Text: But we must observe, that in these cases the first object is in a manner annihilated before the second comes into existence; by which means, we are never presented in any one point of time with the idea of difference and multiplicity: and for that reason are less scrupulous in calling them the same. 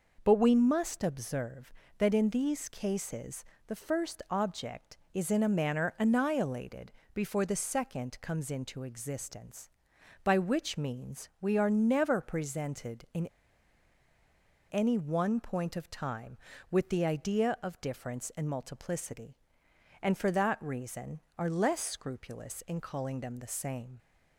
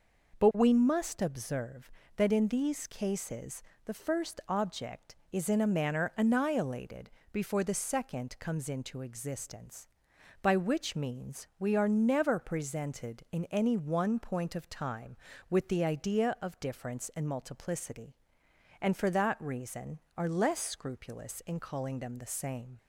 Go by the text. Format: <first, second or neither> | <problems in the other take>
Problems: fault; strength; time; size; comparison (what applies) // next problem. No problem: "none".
second | pauses between "cases" and "the"; slight; at 3.4 s; 0.24 s long; slight in the second // pauses between "annihilated" and "before"; slight; at 6.9 s; 0.22 s long; slight in the second // pauses between "in" and "any"; strong; at 13.2 s; 1.4 s long